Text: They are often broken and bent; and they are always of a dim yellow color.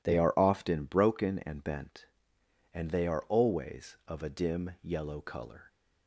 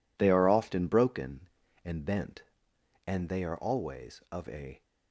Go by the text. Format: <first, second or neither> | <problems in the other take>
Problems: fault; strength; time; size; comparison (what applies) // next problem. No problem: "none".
first | stops before "dim yellow color"; at 4.8 s